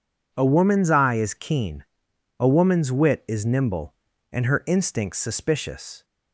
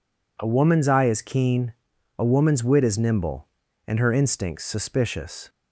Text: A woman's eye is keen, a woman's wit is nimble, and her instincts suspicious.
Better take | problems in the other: neither | none

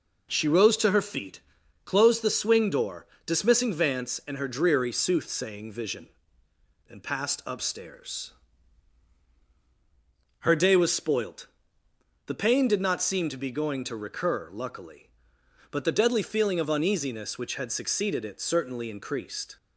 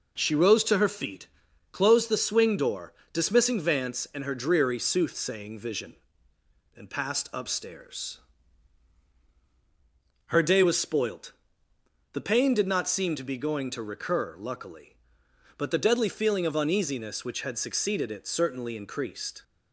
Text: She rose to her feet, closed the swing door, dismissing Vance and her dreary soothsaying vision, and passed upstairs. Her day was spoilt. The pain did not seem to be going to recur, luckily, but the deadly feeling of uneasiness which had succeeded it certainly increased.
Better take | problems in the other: neither | none

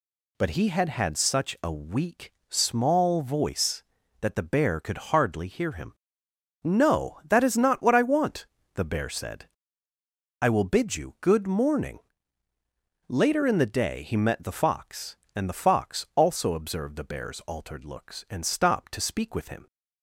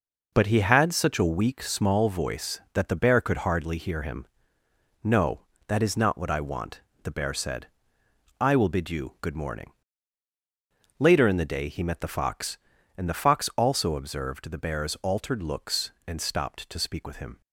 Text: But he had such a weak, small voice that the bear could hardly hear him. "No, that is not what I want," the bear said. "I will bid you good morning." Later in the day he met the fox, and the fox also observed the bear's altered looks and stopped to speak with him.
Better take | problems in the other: second | says "had" twice; at 0.8 s

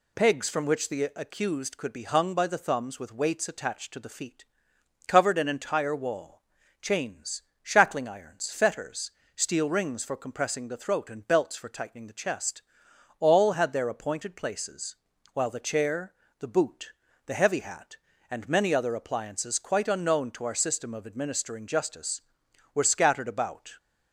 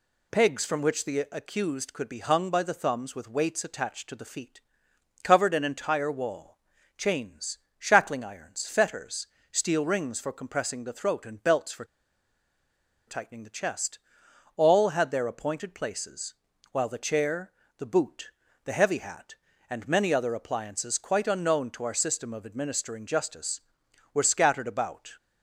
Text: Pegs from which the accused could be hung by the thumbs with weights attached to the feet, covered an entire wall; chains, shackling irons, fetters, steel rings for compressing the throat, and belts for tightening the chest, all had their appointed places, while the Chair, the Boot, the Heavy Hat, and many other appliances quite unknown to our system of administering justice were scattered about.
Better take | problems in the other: first | pauses between "for" and "tightening"; at 11.8 s; 1.2 s long

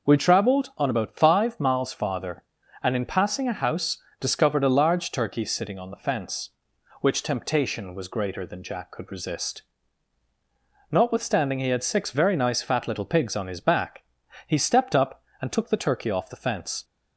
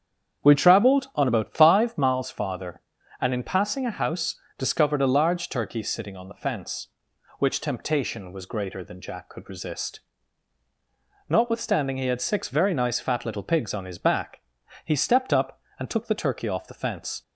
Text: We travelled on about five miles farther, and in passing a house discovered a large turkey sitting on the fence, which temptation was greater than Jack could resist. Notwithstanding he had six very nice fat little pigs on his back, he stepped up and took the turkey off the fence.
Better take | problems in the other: first | starts louder than the rest; strong; until 2.3 s; 8 dB // pauses between "house" and "discovered"; slight; at 4.3 s; 0.22 s long; slight in the first

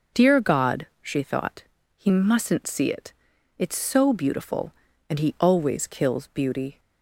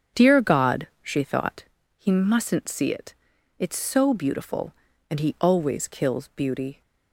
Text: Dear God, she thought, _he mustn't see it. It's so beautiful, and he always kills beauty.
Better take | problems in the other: first | starts louder than the rest; strong; until 1.7 s; 7.5 dB

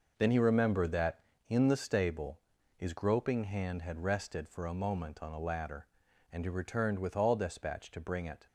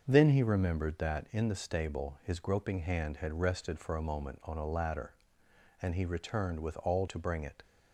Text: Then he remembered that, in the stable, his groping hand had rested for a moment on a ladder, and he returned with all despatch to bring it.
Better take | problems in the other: first | starts louder than the rest; until 1.0 s; 6.5 dB // skips "despatch"; at 7.0 s

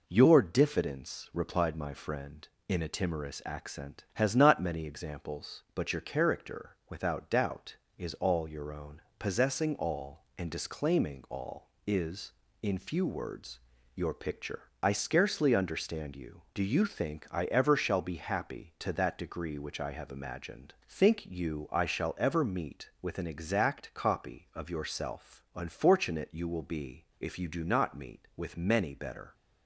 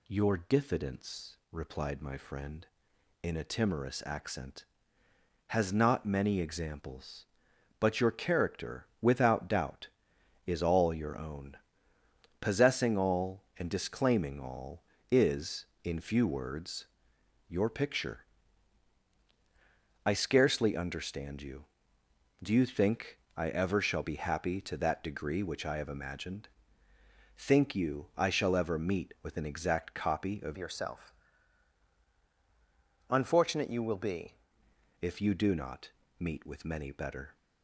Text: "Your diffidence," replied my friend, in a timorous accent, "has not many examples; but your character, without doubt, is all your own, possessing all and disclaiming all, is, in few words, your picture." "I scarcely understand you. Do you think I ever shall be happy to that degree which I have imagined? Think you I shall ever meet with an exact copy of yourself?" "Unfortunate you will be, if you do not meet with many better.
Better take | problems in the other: first | pauses between "think" and "I"; slight; at 23.1 s; 0.18 s long // changes voice from "yourself" to "be"; from 30.5 to 34.3 s; 3.8 s long // pauses between "not" and "meet"; slight; at 35.8 s; 0.30 s long

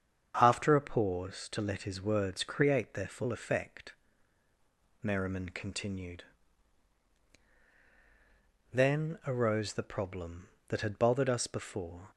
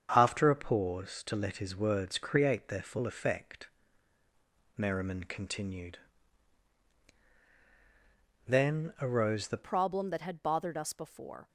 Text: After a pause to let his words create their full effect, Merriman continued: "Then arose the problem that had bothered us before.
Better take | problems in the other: first | starts louder than the rest; strong; until 1.1 s; 7.5 dB; strong in the first // changes voice at "problem"; from 9.6 s on; 1.8 s long

